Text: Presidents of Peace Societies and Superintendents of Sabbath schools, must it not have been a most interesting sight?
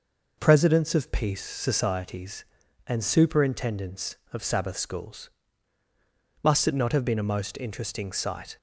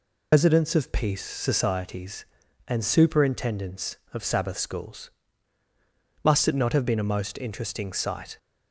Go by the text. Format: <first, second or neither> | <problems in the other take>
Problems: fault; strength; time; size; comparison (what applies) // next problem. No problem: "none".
first | loses the start of "Presidents"; at 0.3 s; 130 ms